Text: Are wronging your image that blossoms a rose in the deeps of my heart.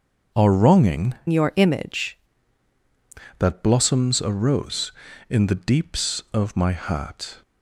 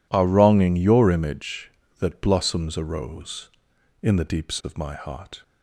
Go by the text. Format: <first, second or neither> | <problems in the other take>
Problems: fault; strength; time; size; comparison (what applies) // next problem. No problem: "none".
second | starts louder than the rest; until 1.5 s; 6.5 dB // changes voice from "your" to "image"; from 1.2 to 2.1 s; 0.9 s long